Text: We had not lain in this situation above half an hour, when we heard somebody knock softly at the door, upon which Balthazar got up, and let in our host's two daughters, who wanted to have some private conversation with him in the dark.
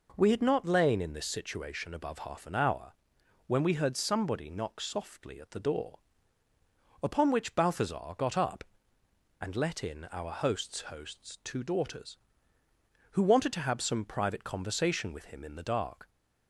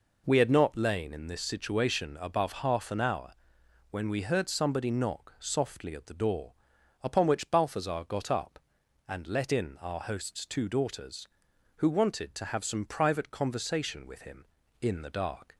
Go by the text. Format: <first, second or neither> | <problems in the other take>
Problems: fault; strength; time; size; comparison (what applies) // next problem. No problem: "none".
second | says "host's" twice; at 10.8 s